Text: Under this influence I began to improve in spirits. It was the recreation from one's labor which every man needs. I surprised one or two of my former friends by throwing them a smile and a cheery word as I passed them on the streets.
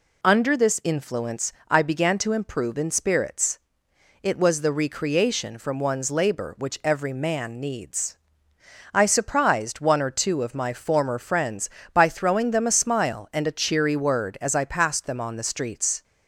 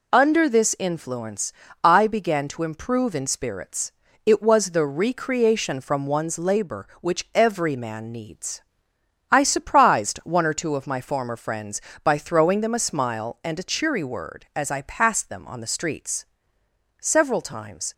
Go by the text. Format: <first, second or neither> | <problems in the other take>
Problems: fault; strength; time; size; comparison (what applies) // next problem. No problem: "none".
first | pauses between "influence" and "I"; slight; at 1.5 s; 0.32 s long; slight in the first // goes on to say "Several times"; noticeable; from 17.0 s on; 0.92 s long